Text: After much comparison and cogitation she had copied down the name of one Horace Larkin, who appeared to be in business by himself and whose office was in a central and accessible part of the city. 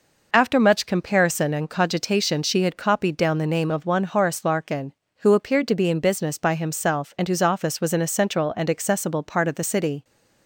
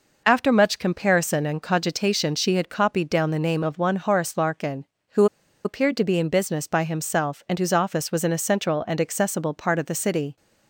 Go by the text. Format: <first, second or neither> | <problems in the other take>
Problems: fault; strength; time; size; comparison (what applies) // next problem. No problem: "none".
first | pauses between "who" and "appeared"; at 5.2 s; 0.39 s long